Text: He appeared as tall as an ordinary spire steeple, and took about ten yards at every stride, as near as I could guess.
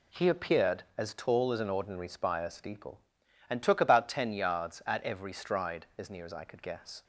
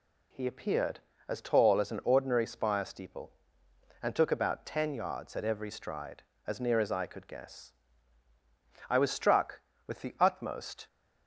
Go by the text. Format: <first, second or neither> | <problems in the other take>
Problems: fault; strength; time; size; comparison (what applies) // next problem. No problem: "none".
first | goes on to say "I was struck with the utmost"; strong; from 8.8 s on; 1.9 s long